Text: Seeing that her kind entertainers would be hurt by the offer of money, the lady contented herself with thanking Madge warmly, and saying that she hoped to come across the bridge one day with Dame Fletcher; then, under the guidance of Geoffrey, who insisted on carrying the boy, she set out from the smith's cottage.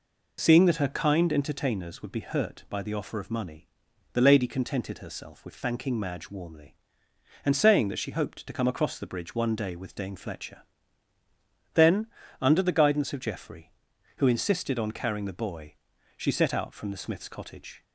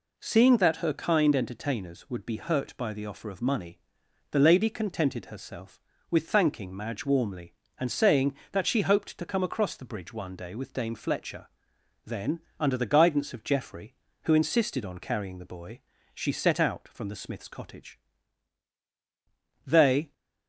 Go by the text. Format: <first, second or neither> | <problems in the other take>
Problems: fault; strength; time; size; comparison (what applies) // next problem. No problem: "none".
first | goes on to say "They"; slight; from 19.6 s on; 0.46 s long